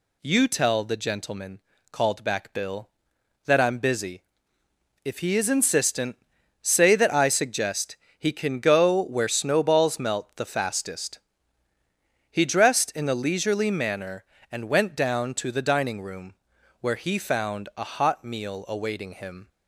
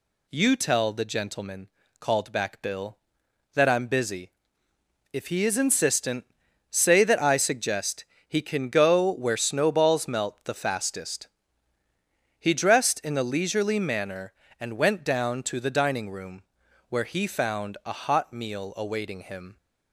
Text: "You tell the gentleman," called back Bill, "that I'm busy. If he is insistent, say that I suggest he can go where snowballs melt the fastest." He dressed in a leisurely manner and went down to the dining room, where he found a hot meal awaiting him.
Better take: neither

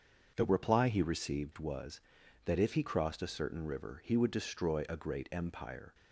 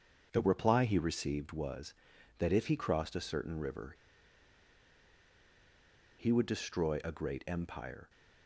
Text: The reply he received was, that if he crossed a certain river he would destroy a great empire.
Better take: first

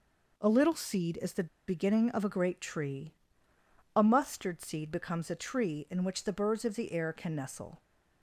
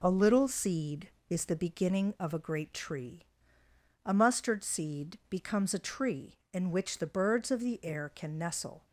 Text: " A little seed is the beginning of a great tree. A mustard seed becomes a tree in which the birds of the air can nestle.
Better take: second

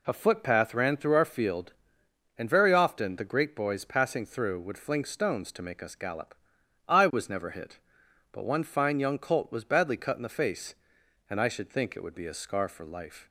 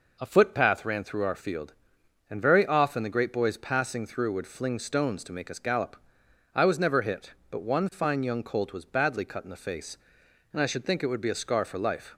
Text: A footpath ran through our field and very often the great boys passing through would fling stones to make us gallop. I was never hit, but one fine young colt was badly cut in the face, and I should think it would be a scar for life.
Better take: neither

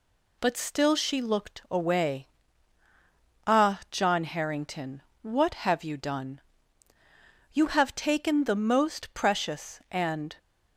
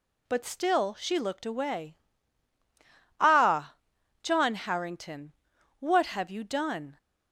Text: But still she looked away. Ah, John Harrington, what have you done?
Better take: second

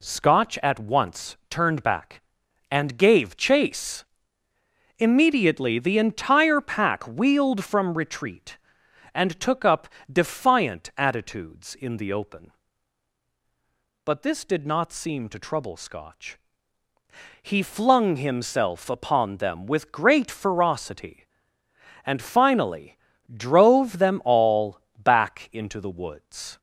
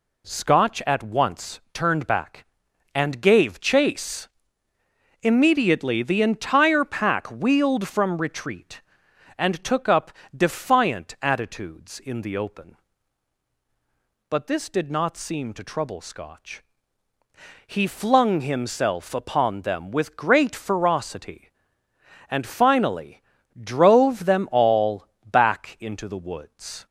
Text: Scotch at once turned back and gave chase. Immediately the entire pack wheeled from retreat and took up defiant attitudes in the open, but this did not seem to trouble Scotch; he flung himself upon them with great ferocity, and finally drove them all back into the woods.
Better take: neither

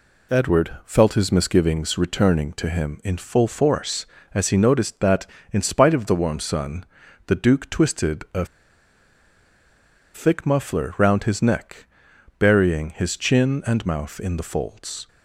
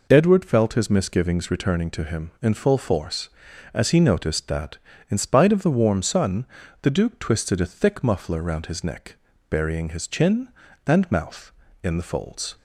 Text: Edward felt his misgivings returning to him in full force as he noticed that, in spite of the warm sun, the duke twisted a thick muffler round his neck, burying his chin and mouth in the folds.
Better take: second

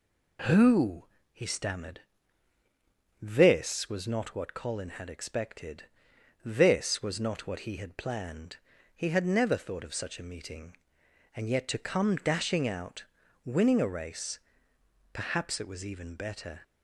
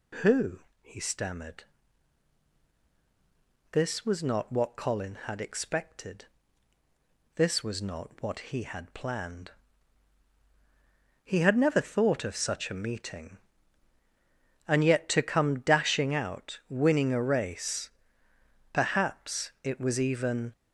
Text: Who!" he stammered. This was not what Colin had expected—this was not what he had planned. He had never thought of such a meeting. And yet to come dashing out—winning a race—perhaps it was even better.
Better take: first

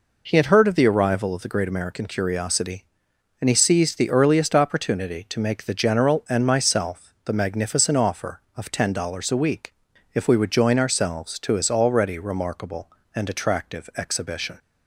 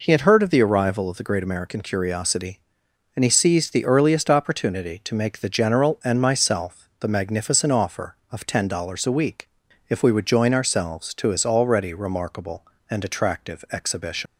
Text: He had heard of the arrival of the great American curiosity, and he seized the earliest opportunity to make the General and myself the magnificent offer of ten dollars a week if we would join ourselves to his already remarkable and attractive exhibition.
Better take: first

